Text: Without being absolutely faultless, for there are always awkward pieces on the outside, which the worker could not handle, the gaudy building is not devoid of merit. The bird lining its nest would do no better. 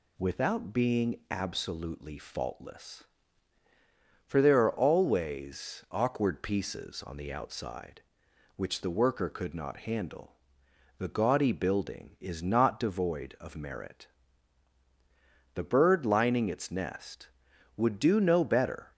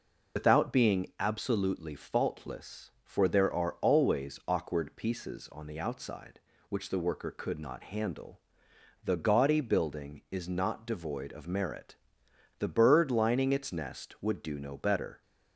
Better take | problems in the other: first | loses the start of "Without"; at 0.3 s; 80 ms

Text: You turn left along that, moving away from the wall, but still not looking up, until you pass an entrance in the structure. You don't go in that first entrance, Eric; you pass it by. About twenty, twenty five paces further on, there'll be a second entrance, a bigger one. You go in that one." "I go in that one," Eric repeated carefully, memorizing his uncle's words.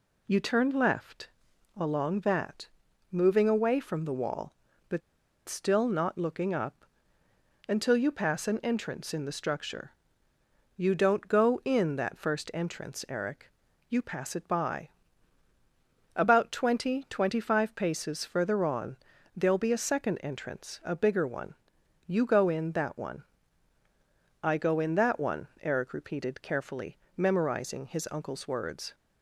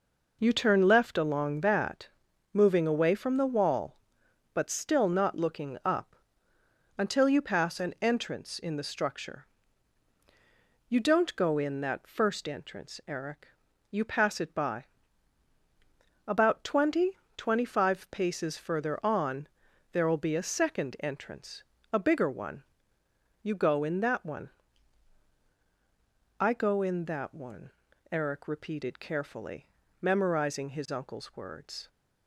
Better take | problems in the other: second | pauses between "left" and "along"; noticeable; at 1.2 s; 0.48 s long // pauses between "but" and "still"; noticeable; at 5.0 s; 0.47 s long

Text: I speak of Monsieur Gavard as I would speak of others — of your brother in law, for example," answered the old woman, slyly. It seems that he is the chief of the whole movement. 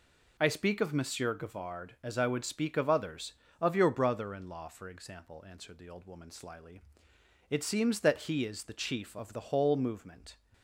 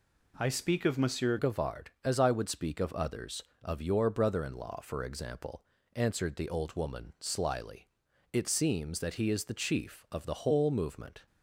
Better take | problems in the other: first | changes voice at "Gavard"; from 1.3 s on; 9.9 s long

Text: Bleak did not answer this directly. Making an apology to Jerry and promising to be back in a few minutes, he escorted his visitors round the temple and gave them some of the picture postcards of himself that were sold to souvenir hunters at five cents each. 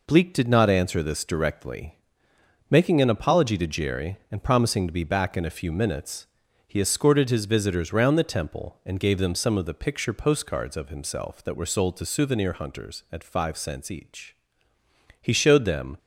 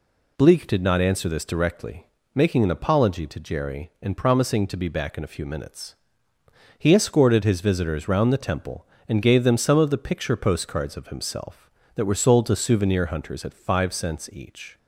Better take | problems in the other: second | goes on to say "He showed them"; noticeable; from 15.2 s on; 0.76 s long

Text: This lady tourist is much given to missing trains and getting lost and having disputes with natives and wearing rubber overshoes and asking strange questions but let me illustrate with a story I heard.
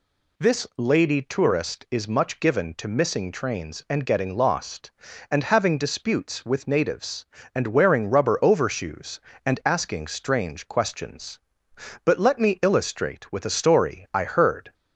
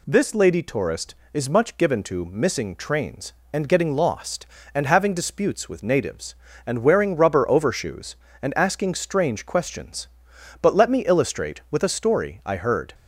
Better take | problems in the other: neither | none

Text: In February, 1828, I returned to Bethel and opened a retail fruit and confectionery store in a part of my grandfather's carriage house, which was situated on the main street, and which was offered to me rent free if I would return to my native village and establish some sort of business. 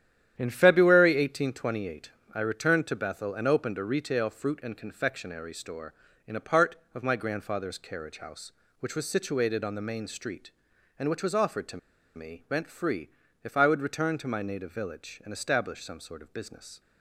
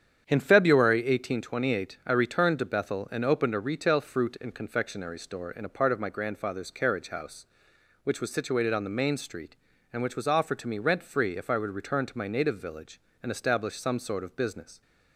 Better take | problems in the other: second | starts louder than the rest; strong; until 1.3 s; 10 dB; strong in the second // pauses between "to" and "me"; at 11.7 s; 0.37 s long // pauses between "free" and "if"; slight; at 13.0 s; 0.34 s long

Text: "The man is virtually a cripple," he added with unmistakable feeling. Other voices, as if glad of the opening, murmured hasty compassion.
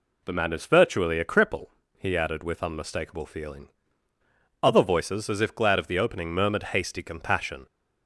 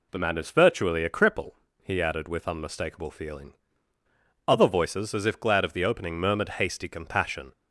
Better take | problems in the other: neither | none

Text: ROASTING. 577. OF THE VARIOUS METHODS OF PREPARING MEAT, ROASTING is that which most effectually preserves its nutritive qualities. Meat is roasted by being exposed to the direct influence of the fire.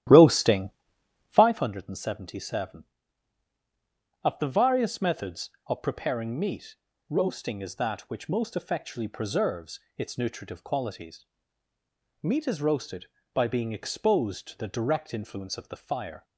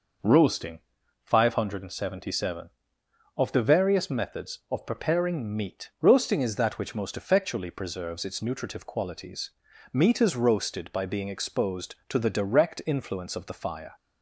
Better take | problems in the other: second | starts louder than the rest; strong; until 1.5 s; 13 dB // pauses between "preserves" and "its"; slight; at 9.7 s; 0.18 s long

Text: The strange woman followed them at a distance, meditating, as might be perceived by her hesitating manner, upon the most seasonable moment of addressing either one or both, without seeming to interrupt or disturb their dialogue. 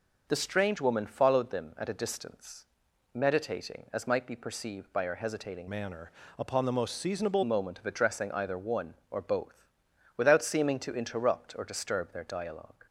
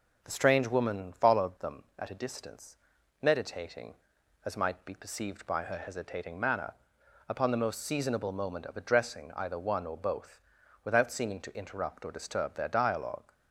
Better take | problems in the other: second | changes voice from "manner" to "seasonable"; from 5.6 to 7.4 s; 1.8 s long

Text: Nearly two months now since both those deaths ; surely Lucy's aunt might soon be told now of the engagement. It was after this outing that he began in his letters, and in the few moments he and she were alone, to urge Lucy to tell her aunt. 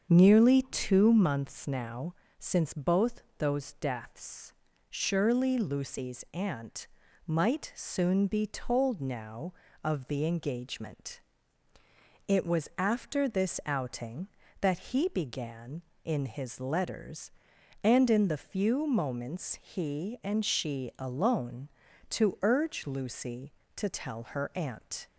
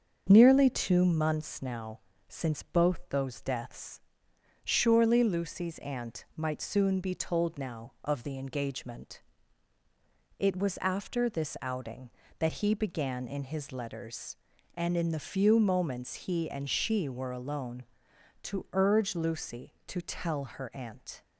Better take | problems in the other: second | starts louder than the rest; until 1.0 s; 7 dB; also in the second // pauses between "now" and "since"; slight; at 2.1 s; 0.24 s long; slight in the second // pauses between "both" and "those"; slight; at 3.2 s; 0.16 s long // pauses between "aunt" and "might"; at 6.8 s; 0.40 s long // skips "were"; at 20.9 s

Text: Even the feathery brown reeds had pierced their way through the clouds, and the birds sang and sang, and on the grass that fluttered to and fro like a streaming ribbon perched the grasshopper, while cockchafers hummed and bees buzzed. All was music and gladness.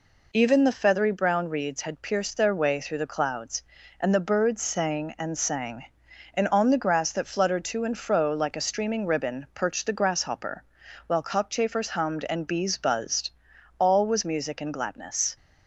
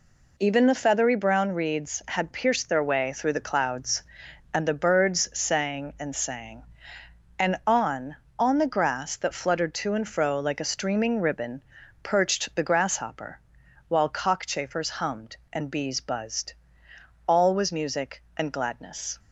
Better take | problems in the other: first | says "on" twice; at 8.3 s // pauses between "ribbon" and "perched"; at 11.6 s; 0.40 s long

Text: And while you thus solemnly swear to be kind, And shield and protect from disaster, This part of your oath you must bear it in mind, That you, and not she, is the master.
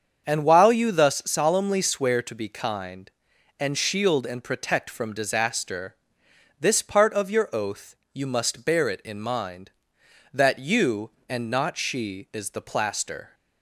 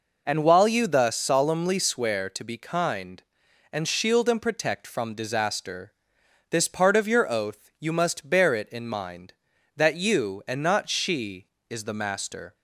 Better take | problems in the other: second | starts louder than the rest; strong; until 1.3 s; 7 dB // pauses between "oath" and "you"; slight; at 7.9 s; 0.16 s long // says "plaster" for "master"; at 12.6 s

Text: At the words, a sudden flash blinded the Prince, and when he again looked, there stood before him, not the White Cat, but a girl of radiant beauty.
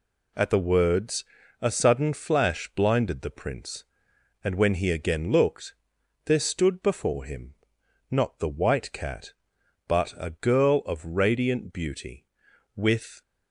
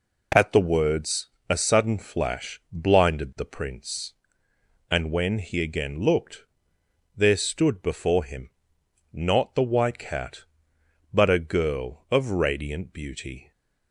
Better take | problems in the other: second | goes on to say "With"; slight; from 12.7 s on; 0.46 s long

